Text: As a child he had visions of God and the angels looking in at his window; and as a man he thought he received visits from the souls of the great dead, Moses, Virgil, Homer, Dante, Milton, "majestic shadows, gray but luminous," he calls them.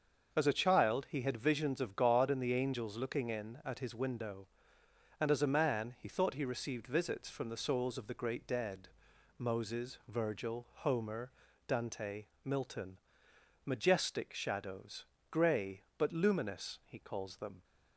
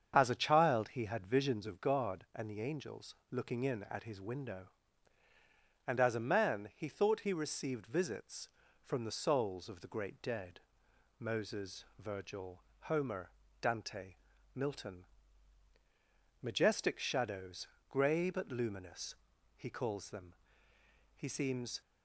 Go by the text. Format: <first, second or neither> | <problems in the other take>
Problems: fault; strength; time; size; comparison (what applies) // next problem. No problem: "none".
first | starts louder than the rest; strong; until 1.1 s; 7.5 dB; also in the first // pauses between "angels" and "looking"; slight; at 3.1 s; 0.18 s long // goes on to say "He seems"; noticeable; from 21.1 s on; 0.64 s long